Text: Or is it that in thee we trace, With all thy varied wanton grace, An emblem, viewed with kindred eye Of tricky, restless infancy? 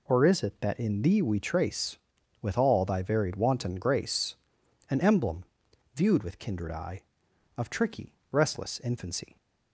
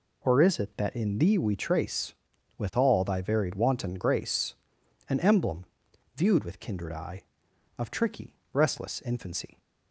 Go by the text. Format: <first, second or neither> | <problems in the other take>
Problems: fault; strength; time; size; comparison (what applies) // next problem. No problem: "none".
neither | none